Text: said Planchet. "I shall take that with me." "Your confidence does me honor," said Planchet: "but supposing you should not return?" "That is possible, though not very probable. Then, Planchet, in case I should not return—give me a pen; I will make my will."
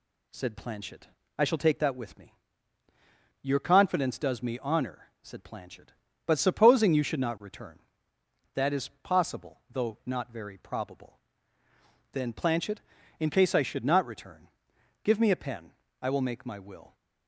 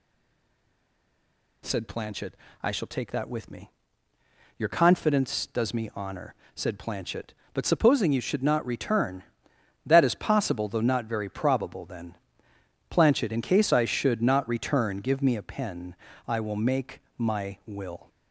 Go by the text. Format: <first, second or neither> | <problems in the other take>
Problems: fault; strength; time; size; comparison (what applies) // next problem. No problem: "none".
first | stays silent before the first word; noticeable; until 1.6 s; 1.6 s long // pauses between "make" and "my"; slight; at 17.0 s; 0.16 s long